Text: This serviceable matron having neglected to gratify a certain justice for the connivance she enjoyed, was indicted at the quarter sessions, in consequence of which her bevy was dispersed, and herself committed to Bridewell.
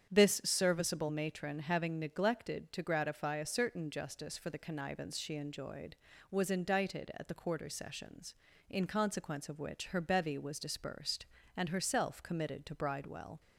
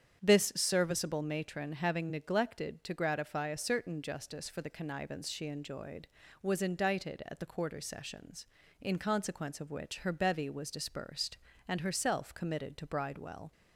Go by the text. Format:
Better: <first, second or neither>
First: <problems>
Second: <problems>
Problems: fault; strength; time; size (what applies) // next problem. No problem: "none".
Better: neither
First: starts louder than the rest; strong; until 1.1 s; 8.5 dB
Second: starts louder than the rest; strong; until 1.2 s; 8.5 dB